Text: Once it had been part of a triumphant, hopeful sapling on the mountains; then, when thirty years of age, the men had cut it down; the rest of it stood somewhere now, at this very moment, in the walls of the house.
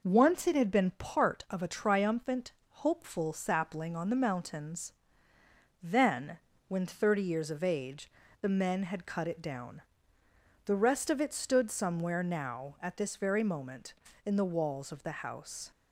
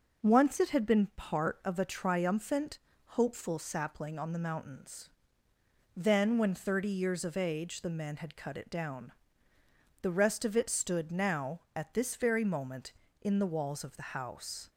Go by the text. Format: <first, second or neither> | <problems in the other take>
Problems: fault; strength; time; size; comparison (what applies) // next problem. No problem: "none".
first | skips "somewhere"; at 11.1 s